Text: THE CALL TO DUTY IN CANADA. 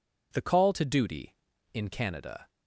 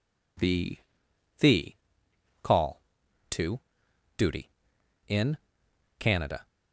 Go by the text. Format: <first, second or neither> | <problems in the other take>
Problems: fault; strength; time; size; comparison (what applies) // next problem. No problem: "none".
first | says "THE" twice; at 1.3 s // pauses between "TO" and "DUTY"; noticeable; at 3.5 s; 0.60 s long // pauses between "IN" and "CANADA"; noticeable; at 5.3 s; 0.63 s long